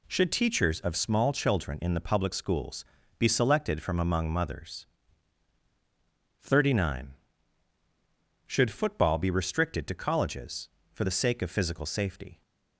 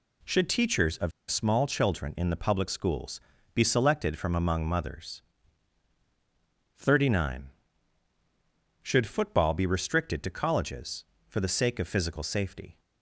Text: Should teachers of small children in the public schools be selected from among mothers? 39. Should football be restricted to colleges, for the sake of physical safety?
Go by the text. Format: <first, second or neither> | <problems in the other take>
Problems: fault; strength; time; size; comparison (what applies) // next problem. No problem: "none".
first | pauses between "of" and "small"; slight; at 1.1 s; 0.19 s long // pauses between "schools" and "be"; slight; at 3.2 s; 0.34 s long; slight in the first